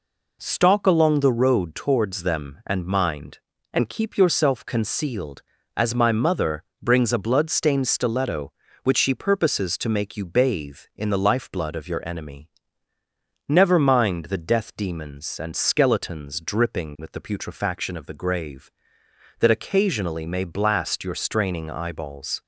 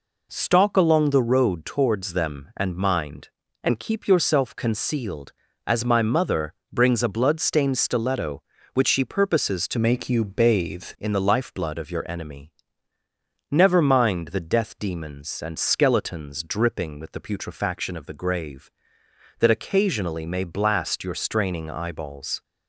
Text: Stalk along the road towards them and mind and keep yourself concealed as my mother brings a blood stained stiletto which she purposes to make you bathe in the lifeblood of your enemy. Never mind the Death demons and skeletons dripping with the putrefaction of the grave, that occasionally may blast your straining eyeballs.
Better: first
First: pauses between "mother" and "brings"; slight; at 6.6 s; 0.16 s long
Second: pauses between "mother" and "brings"; slight; at 6.5 s; 0.16 s long // changes voice from "make" to "bathe"; from 9.7 to 10.8 s; 1.1 s long

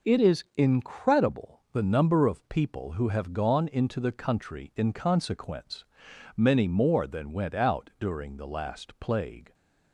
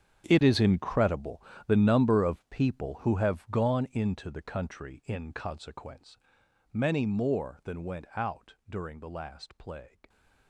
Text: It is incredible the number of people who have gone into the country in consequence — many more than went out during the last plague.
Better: first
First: none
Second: gets quieter; strong; throughout; 17.5 dB // pauses between "incredible" and "the"; slight; at 1.4 s; 0.28 s long

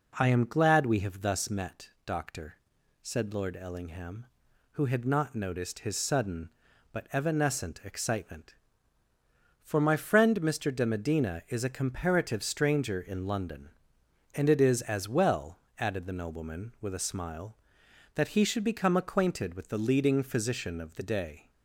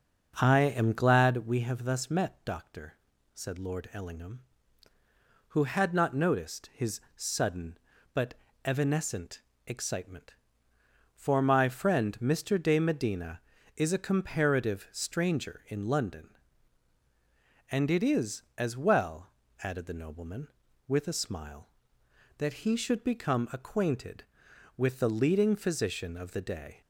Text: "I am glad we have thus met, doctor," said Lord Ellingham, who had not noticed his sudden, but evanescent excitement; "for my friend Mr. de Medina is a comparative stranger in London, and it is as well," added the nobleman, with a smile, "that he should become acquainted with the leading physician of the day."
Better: first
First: none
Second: starts louder than the rest; until 1.5 s; 6.5 dB // pauses between "his" and "sudden"; slight; at 6.9 s; 0.16 s long // pauses between "but" and "evanescent"; slight; at 8.3 s; 0.30 s long // pauses between "evanescent" and "excitement"; slight; at 9.4 s; 0.22 s long

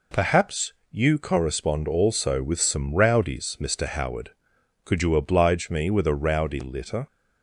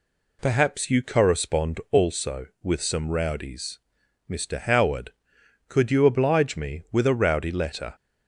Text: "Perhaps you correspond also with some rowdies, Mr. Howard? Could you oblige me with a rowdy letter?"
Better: second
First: pauses between "Perhaps" and "you"; slight; at 0.7 s; 0.16 s long // says "litter" for "letter"; at 6.6 s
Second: none

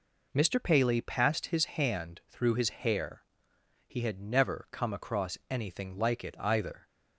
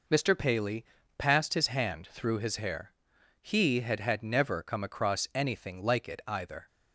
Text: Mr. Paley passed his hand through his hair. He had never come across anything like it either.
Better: first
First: none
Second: pauses between "Paley" and "passed"; slight; at 0.8 s; 0.34 s long // says "had" twice; at 4.0 s

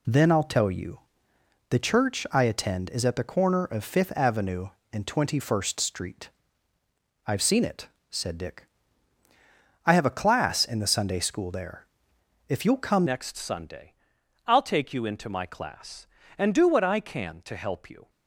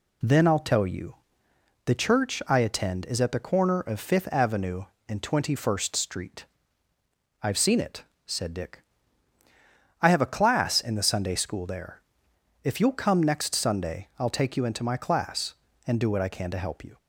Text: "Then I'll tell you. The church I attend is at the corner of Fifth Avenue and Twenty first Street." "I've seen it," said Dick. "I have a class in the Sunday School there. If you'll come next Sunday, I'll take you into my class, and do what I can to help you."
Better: second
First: changes voice at "next"; from 13.0 s on; 5.0 s long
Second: none

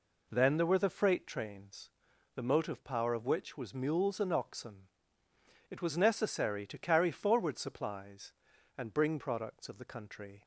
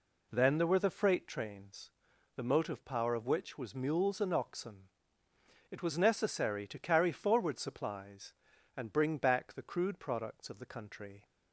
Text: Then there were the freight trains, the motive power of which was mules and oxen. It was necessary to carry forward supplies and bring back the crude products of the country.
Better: second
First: skips "back the crude"; at 9.1 s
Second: none

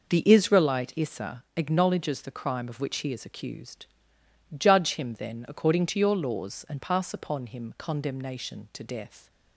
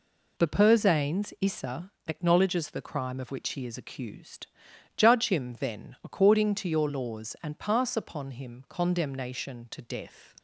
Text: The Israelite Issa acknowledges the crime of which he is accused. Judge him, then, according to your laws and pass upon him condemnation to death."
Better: first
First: none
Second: says "Persanes" for "Israelite"; at 0.4 s // pauses between "Issa" and "acknowledges"; slight; at 1.9 s; 0.16 s long

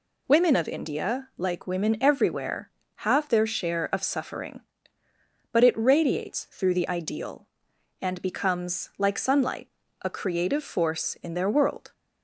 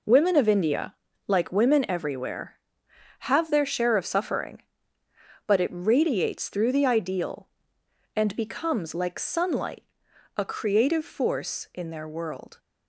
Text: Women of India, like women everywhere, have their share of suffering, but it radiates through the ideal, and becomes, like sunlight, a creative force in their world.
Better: neither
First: none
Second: none

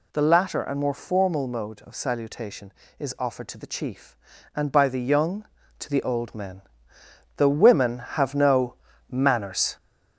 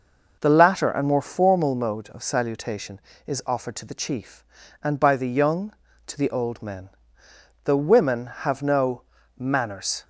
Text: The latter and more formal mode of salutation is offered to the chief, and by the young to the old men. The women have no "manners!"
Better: second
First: gets louder; noticeable; throughout; 4 dB // pauses between "no" and "manners"; slight; at 8.7 s; 0.34 s long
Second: pauses between "no" and "manners"; slight; at 9.0 s; 0.34 s long

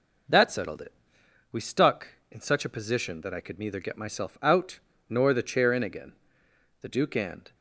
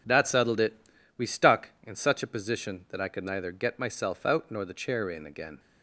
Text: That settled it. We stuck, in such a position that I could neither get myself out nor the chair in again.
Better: second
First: pauses between "out" and "nor"; slight; at 4.8 s; 0.28 s long // goes on to say "The Duke and"; noticeable; from 6.8 s on; 0.74 s long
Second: none

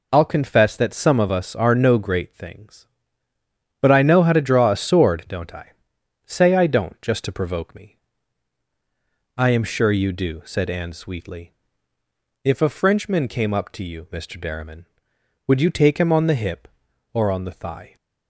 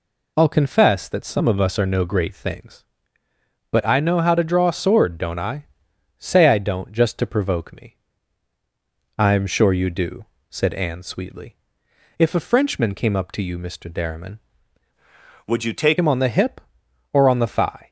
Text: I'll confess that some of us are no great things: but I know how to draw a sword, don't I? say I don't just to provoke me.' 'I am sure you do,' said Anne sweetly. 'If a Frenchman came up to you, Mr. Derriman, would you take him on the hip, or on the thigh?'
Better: first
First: none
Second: changes voice from "would" to "take"; from 15.4 to 15.9 s; 0.5 s long

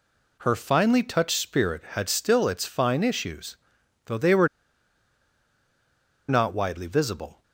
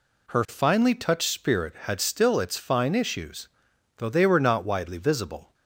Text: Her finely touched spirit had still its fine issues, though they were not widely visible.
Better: second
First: pauses between "were" and "not"; strong; at 4.4 s; 1.8 s long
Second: none

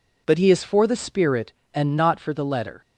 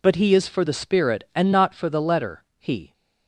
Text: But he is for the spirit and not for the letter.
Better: first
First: none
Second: goes on to say "He"; slight; from 2.5 s on; 0.34 s long

